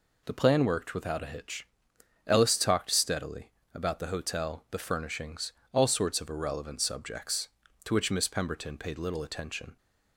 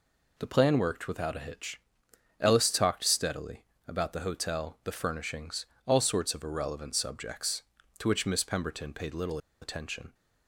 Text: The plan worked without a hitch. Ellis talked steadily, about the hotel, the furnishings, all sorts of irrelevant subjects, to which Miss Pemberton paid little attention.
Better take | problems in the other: first | pauses between "little" and "attention"; slight; at 9.3 s; 0.23 s long

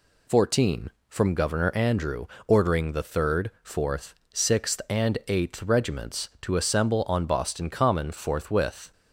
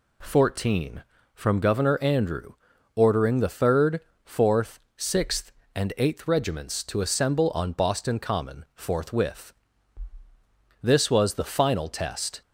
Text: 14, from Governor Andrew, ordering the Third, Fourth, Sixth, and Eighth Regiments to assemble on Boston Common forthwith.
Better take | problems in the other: first | goes on to say "This was the final test"; from 10.8 s on; 1.6 s long

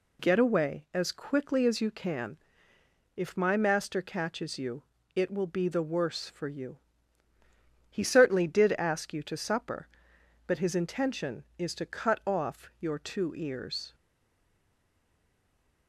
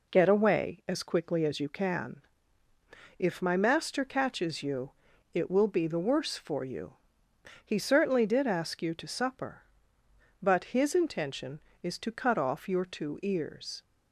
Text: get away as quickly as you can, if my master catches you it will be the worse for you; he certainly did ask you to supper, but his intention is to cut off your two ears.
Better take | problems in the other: second | pauses between "you" and "it"; slight; at 4.8 s; 0.30 s long; also in the second // stays silent after the last word; noticeable; from 13.9 s on; 1.9 s long

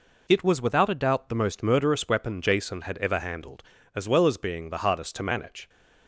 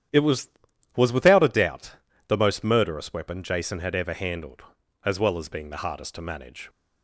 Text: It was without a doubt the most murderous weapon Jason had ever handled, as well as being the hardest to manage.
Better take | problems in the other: first | starts louder than the rest; strong; until 1.5 s; 10 dB // says "was" twice; at 0.9 s // pauses between "doubt" and "the"; slight; at 1.9 s; 0.30 s long

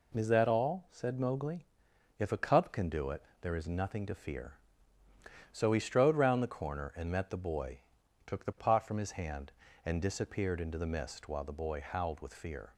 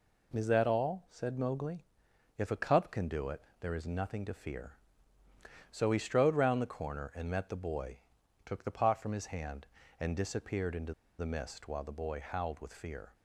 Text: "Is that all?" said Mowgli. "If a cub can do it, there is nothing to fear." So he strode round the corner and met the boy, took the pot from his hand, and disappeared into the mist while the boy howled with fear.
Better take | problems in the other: first | pauses between "into" and "the"; slight; at 10.9 s; 0.25 s long

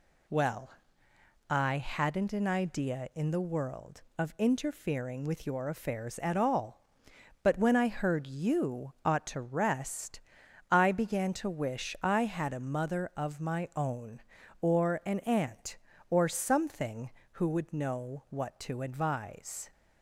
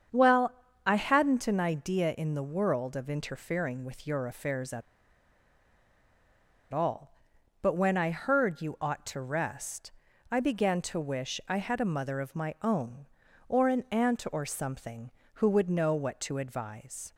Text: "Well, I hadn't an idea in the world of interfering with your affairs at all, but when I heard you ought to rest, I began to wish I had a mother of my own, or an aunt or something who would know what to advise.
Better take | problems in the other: first | starts louder than the rest; strong; until 1.4 s; 7.5 dB // pauses between "at" and "all"; strong; at 4.8 s; 1.9 s long

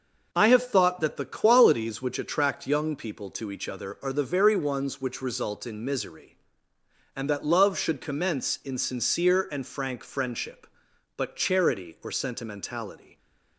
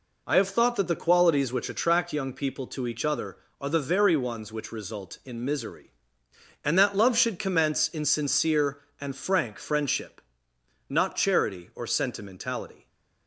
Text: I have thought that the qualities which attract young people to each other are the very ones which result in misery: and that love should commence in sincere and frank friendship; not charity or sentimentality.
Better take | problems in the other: second | says "but" for "not"; at 11.1 s

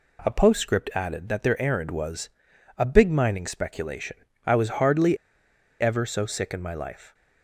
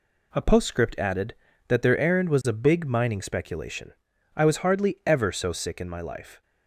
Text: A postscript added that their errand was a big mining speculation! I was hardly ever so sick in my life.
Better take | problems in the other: second | pauses between "was" and "a"; noticeable; at 2.2 s; 0.48 s long // pauses between "hardly" and "ever"; noticeable; at 5.1 s; 0.64 s long

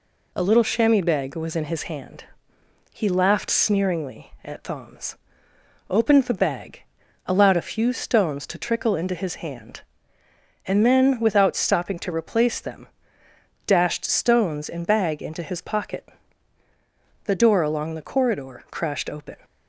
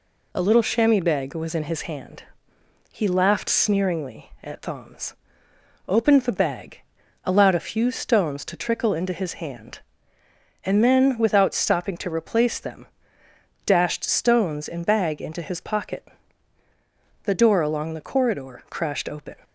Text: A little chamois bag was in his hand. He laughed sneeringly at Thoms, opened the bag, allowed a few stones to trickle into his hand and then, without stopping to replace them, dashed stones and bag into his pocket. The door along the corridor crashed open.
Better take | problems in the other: neither | none

